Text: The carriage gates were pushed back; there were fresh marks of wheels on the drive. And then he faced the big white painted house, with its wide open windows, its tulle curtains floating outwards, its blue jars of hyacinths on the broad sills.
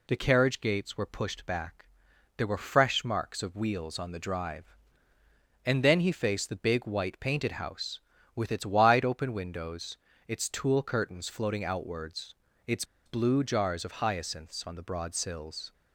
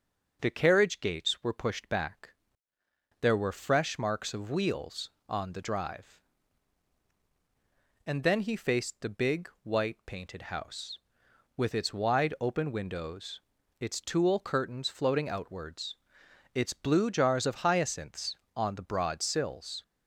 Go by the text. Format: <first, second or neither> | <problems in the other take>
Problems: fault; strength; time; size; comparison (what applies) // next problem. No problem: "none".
second | pauses between "its" and "blue"; slight; at 12.8 s; 0.22 s long